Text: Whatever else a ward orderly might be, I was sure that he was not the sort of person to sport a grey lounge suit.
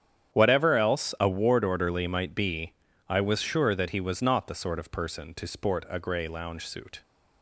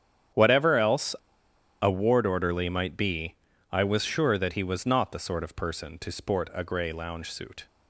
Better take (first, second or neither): first